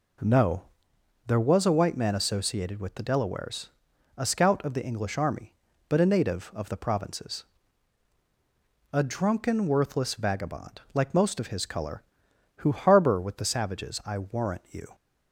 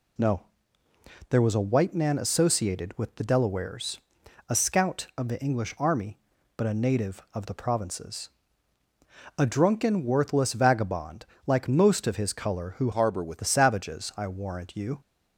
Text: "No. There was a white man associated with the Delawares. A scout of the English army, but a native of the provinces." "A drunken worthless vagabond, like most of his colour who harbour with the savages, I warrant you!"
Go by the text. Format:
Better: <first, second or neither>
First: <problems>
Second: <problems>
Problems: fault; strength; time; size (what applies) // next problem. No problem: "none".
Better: first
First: none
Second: changes voice from "harbour" to "with"; from 12.9 to 13.3 s; 0.4 s long